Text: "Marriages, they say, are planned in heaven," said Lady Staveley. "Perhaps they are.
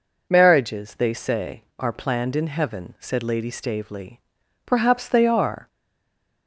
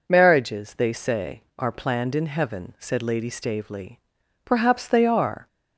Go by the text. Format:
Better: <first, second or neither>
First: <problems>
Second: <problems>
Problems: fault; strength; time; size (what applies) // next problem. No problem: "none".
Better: second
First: stays silent after the last word; slight; from 5.6 s on; 0.8 s long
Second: none